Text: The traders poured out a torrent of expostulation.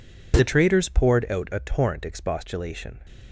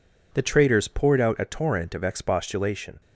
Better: second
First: skips "of"; at 2.0 s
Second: none

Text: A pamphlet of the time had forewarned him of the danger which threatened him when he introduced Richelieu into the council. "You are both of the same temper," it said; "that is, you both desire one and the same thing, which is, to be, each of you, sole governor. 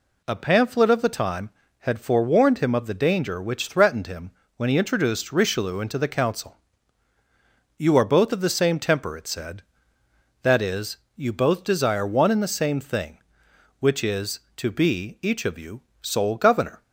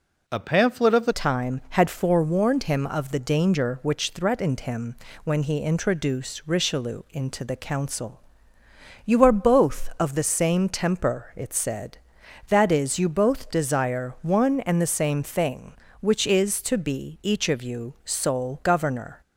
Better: first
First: pauses between "him" and "when"; slight; at 4.3 s; 0.26 s long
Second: changes voice at "time"; from 1.1 s on; 18.1 s long // pauses between "him" and "when"; slight; at 4.9 s; 0.30 s long

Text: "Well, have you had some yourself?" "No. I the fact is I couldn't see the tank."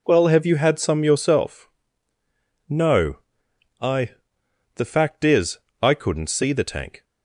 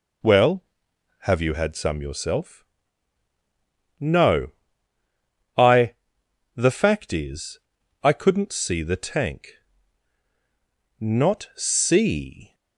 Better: first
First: pauses between "I" and "the"; noticeable; at 4.1 s; 0.64 s long // pauses between "is" and "I"; slight; at 5.5 s; 0.22 s long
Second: pauses between "I" and "the"; noticeable; at 5.9 s; 0.61 s long // pauses between "is" and "I"; at 7.5 s; 0.44 s long // goes on to say "Not see"; from 10.9 s on; 1.5 s long

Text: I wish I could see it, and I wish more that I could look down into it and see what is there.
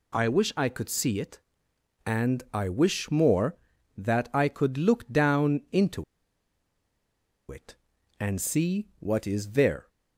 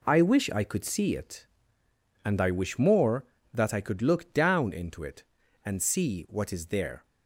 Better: second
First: pauses between "into" and "it"; strong; at 6.0 s; 1.4 s long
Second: none

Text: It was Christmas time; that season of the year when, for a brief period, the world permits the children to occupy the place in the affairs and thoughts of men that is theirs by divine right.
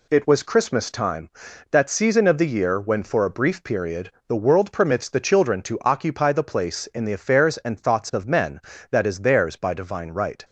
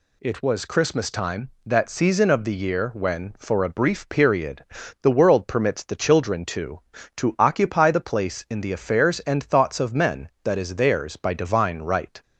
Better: first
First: none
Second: says "to" twice; at 7.1 s

